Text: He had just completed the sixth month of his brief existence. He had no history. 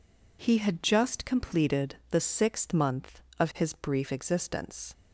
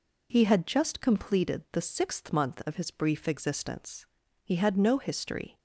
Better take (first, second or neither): second